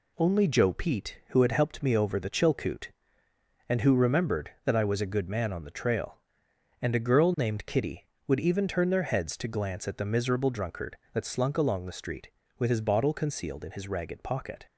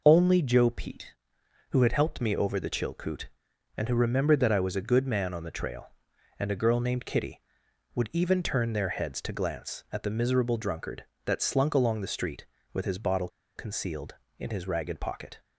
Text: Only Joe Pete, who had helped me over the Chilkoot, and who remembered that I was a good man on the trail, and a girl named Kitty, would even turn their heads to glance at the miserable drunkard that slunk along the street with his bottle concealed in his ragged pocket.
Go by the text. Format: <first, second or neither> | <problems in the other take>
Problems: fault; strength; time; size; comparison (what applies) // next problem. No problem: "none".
first | pauses between "bottle" and "concealed"; slight; at 13.2 s; 0.27 s long